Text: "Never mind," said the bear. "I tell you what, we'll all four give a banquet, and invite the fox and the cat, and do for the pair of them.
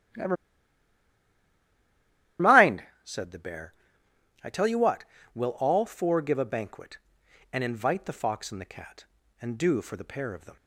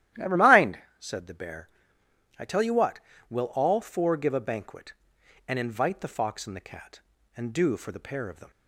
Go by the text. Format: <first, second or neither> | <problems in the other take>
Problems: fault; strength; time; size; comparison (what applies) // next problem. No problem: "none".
second | starts louder than the rest; strong; until 3.3 s; 12.5 dB; strong in the second // pauses between "Never" and "mind"; strong; at 0.3 s; 2.0 s long